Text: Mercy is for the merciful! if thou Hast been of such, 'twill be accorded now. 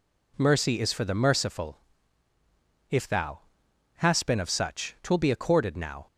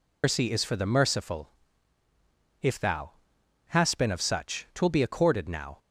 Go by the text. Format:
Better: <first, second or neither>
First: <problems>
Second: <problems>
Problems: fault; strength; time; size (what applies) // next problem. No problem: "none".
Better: first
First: pauses between "thou" and "Hast"; noticeable; at 3.3 s; 0.60 s long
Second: loses the start of "Mercy"; at 0.2 s; 185 ms // pauses between "thou" and "Hast"; noticeable; at 3.1 s; 0.60 s long